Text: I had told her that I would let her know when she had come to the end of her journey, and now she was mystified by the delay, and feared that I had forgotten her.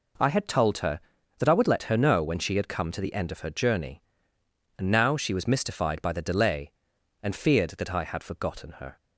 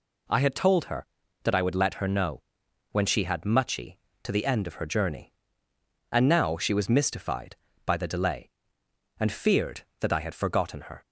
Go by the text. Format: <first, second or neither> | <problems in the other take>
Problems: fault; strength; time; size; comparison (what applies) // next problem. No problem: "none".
first | pauses between "know" and "when"; noticeable; at 2.4 s; 0.50 s long // says "muchy" for "come"; at 3.4 s